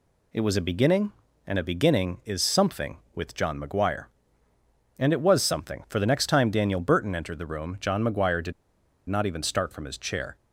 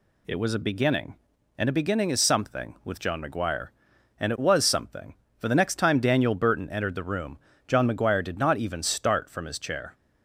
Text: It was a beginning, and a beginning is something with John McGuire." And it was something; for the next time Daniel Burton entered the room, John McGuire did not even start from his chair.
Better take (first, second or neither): second